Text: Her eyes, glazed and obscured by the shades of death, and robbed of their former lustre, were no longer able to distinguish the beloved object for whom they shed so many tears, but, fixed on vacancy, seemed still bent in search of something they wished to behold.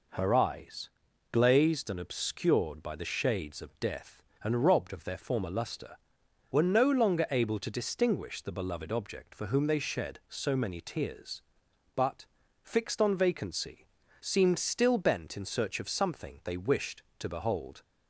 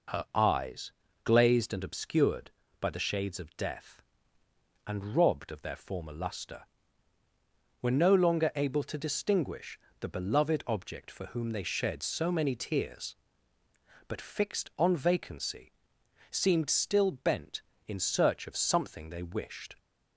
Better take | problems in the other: first | pauses between "distinguish" and "the"; slight; at 9.7 s; 0.22 s long // stops before "to behold"; at 19.7 s

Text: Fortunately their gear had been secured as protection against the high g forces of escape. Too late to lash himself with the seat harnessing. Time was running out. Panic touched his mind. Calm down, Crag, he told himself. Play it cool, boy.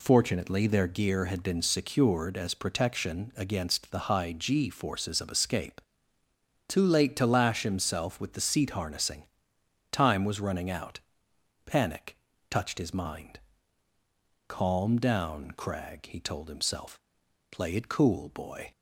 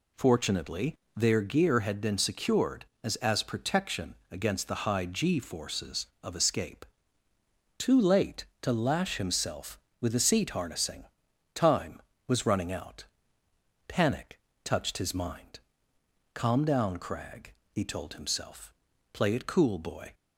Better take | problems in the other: first | pauses between "Fortunately" and "their"; slight; at 0.9 s; 0.20 s long // says "as" twice; at 3.1 s // pauses between "protection" and "against"; slight; at 4.1 s; 0.16 s long // pauses between "Panic" and "touched"; slight; at 14.3 s; 0.24 s long; slight in the first

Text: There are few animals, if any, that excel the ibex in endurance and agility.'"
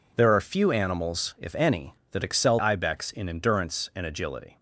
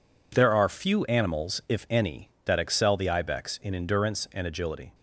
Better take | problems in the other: second | skips "the"; at 2.5 s

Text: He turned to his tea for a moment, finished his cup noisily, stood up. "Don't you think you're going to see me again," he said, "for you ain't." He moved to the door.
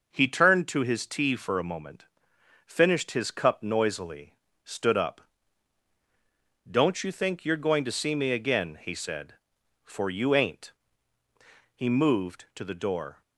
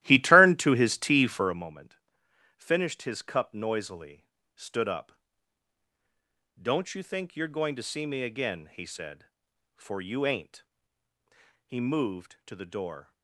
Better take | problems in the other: first | starts louder than the rest; strong; until 1.6 s; 14.5 dB

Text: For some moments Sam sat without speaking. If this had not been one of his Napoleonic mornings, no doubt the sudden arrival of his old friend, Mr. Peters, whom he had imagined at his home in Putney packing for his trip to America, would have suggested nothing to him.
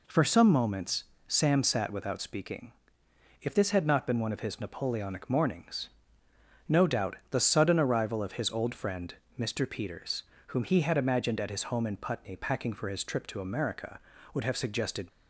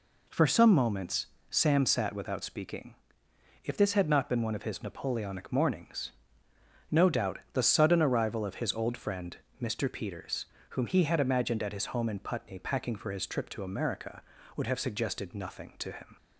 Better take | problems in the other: second | pauses between "moments" and "Sam"; slight; at 1.0 s; 0.24 s long; slight in the second // stops before "nothing to him"; at 15.0 s

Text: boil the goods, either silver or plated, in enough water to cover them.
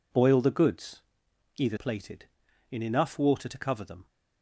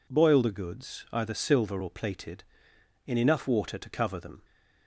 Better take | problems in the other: second | skips "silver or"; at 1.7 s

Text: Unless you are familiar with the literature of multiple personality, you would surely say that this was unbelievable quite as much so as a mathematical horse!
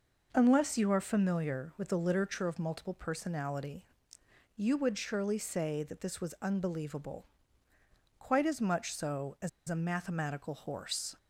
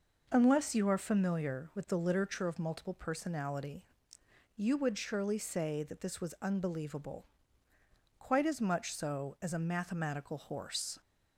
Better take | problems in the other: second | pauses between "unbelievable" and "quite"; noticeable; at 7.2 s; 0.94 s long; noticeable in the second // pauses between "as" and "a"; slight; at 9.4 s; 0.19 s long

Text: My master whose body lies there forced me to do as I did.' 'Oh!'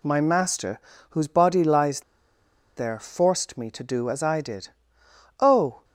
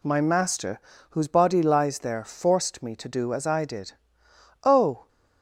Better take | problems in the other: second | pauses between "master" and "whose"; slight; at 0.8 s; 0.30 s long; slight in the second // pauses between "lies" and "there"; noticeable; at 2.0 s; 0.76 s long

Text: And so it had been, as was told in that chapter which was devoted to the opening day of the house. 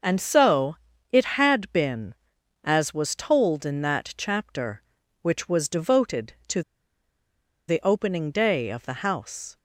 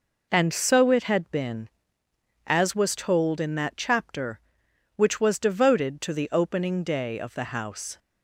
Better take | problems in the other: second | pauses between "so" and "it"; slight; at 0.7 s; 0.36 s long // pauses between "to" and "the"; at 6.6 s; 1.0 s long

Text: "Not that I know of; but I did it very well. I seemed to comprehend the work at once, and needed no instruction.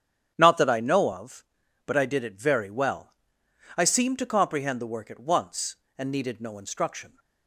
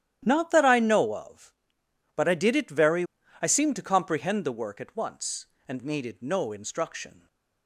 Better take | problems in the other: first | starts louder than the rest; strong; until 1.2 s; 11 dB; strong in the first // skips "well"; at 3.2 s

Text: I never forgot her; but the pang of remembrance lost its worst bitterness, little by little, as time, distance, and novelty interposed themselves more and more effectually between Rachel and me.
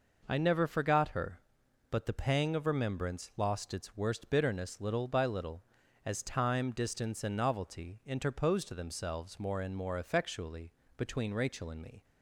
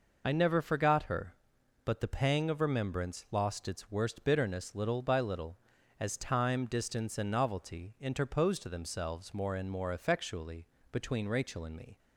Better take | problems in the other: first | loses the start of "I"; at 0.2 s; 70 ms // pauses between "effectually" and "between"; slight; at 10.6 s; 0.24 s long; slight in the first

